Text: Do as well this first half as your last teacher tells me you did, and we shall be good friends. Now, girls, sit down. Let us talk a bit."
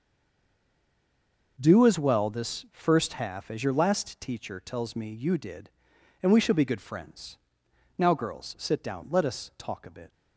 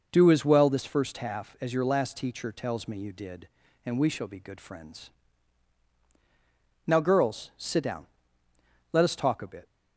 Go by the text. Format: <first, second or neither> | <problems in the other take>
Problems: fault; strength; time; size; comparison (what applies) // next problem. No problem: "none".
second | stays silent before the first word; noticeable; until 1.5 s; 1.5 s long